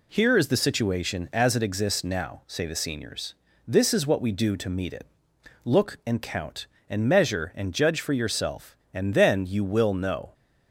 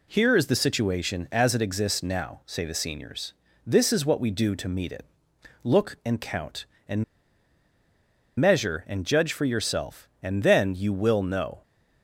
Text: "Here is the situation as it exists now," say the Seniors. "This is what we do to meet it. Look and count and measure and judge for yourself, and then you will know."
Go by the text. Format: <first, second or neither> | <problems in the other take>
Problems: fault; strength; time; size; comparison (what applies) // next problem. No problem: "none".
first | pauses between "and" and "measure"; strong; at 7.0 s; 1.3 s long